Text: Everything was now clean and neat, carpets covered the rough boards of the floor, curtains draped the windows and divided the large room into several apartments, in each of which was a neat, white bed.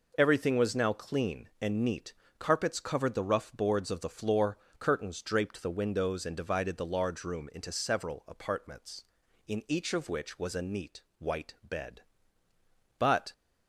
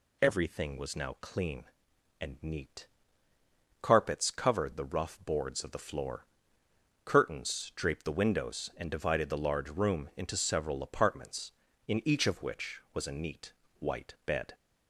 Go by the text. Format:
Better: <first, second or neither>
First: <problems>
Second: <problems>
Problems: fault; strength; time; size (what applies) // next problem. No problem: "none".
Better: second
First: goes on to say "But"; slight; from 12.9 s on; 0.34 s long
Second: none